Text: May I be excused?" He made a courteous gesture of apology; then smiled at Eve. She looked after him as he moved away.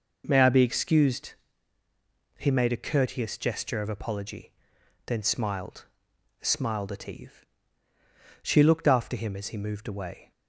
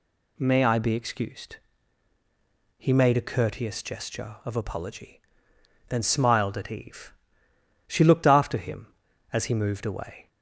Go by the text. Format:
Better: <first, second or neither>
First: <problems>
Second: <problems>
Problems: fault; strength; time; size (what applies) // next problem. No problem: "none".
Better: second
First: says "smiled" twice; at 6.4 s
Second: none